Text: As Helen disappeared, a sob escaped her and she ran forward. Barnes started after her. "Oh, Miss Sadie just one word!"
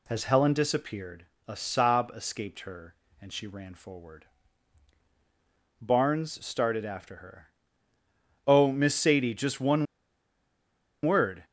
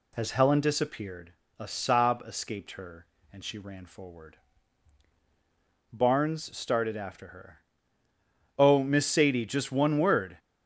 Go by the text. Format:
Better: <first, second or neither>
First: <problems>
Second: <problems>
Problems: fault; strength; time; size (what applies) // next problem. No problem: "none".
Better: second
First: pauses between "one" and "word"; at 9.8 s; 1.1 s long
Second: none